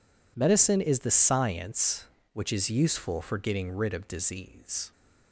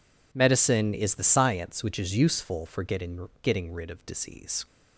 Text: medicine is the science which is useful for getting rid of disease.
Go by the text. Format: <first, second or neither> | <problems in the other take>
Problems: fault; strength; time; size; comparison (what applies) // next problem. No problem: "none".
first | says "getting" twice; at 3.4 s